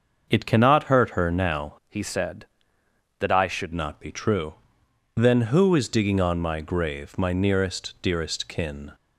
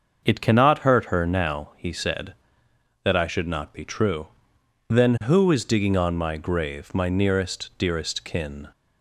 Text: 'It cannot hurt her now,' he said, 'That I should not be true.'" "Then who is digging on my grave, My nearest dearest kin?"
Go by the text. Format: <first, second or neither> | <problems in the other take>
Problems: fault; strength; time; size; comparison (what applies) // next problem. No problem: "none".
second | starts louder than the rest; until 1.3 s; 6.5 dB; also in the second // changes voice from "he" to "should"; from 1.8 to 3.7 s; 1.9 s long